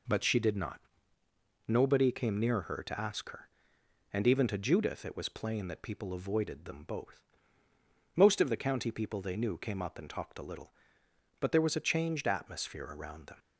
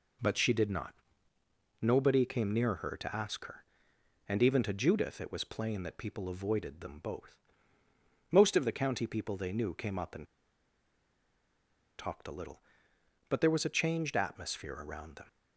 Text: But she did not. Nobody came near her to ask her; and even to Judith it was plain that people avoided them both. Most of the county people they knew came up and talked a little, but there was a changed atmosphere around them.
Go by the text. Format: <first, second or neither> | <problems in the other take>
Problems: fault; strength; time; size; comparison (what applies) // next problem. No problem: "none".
first | pauses between "and" and "talked"; strong; at 10.2 s; 1.7 s long